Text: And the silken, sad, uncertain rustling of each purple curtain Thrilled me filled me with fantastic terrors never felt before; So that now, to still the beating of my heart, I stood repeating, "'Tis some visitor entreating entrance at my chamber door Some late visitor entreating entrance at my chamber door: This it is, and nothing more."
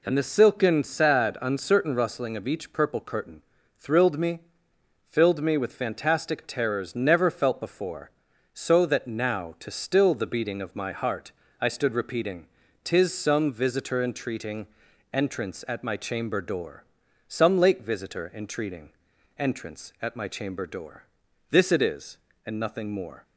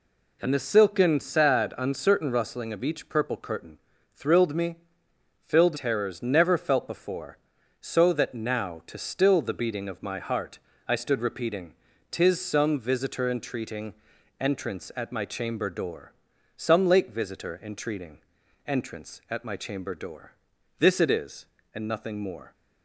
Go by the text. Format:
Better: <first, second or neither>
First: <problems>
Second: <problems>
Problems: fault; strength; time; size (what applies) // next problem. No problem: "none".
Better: first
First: pauses between "curtain" and "Thrilled"; slight; at 3.4 s; 0.36 s long // pauses between "me" and "filled"; noticeable; at 4.3 s; 0.70 s long // pauses between "entreating" and "entrance"; noticeable; at 14.6 s; 0.48 s long // pauses between "door" and "Some"; at 16.8 s; 0.44 s long // pauses between "entreating" and "entrance"; noticeable; at 18.9 s; 0.48 s long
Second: pauses between "curtain" and "Thrilled"; slight; at 3.7 s; 0.36 s long // pauses between "me" and "filled"; noticeable; at 4.7 s; 0.70 s long // skips "me with fantastic"; at 5.7 s // pauses between "entreating" and "entrance"; noticeable; at 13.9 s; 0.48 s long // pauses between "door" and "Some"; at 16.1 s; 0.44 s long // pauses between "entreating" and "entrance"; noticeable; at 18.1 s; 0.48 s long